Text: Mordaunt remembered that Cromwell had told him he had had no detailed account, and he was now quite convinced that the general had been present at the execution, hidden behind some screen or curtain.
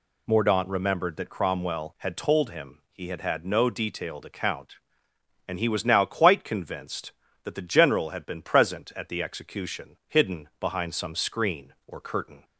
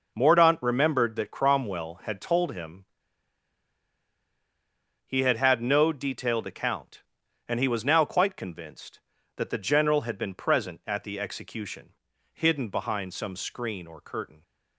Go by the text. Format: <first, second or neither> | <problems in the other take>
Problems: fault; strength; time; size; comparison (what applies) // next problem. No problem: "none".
first | pauses between "him" and "he"; strong; at 2.8 s; 2.2 s long